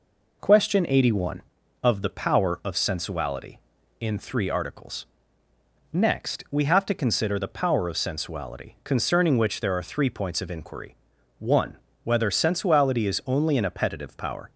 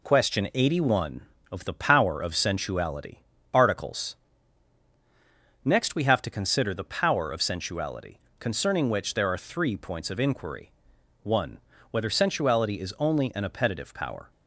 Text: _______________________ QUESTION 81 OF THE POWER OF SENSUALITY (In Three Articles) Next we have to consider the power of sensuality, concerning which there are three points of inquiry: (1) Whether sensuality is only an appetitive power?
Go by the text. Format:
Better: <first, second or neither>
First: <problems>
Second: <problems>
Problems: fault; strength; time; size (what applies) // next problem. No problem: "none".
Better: first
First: none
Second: skips "In Three"; at 3.3 s